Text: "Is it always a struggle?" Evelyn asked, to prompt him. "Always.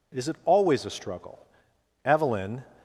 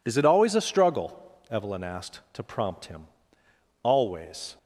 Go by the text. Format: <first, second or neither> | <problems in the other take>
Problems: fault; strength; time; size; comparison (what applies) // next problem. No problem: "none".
second | stops before "asked to prompt him Always"; at 2.7 s